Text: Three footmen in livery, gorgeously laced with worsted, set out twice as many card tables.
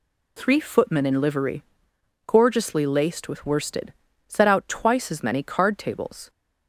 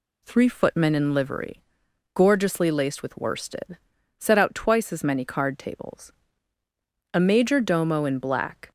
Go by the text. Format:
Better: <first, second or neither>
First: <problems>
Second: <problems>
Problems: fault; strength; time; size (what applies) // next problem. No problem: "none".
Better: first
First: none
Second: goes on to say "A major domo in black"; from 7.1 s on; 1.5 s long